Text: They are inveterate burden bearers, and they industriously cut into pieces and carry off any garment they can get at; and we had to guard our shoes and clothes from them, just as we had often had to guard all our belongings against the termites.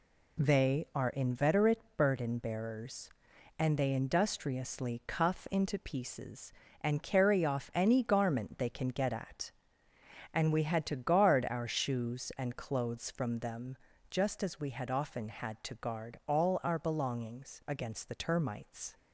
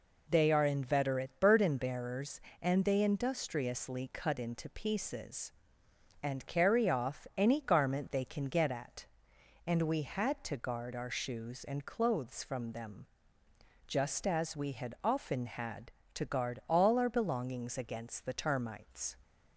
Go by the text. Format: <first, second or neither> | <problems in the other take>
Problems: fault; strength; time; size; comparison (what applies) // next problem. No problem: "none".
second | pauses between "inveterate" and "burden"; slight; at 1.8 s; 0.16 s long // says "cuff" for "cut"; at 5.0 s